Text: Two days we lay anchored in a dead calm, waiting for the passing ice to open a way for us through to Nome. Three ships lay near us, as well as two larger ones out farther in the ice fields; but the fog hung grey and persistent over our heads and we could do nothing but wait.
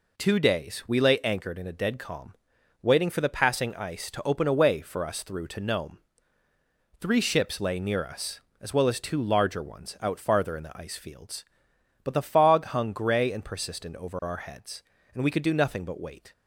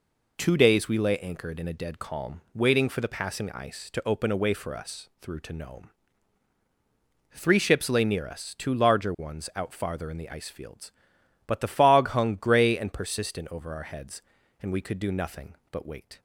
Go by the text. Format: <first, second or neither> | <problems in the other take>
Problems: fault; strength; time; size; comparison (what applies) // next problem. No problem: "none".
first | skips "as well as"; at 8.5 s